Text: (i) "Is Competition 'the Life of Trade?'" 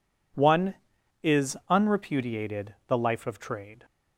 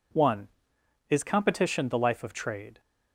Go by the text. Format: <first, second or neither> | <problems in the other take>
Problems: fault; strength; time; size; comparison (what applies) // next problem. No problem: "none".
second | says "Unrepudiated" for "Competition"; at 1.7 s